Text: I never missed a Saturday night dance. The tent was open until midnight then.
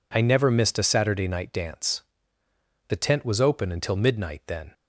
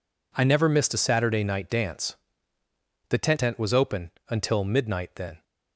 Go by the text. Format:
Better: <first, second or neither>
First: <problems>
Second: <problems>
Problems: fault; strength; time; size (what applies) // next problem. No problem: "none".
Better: first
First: none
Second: says "tent" twice; at 3.4 s // pauses between "open" and "until"; slight; at 4.0 s; 0.20 s long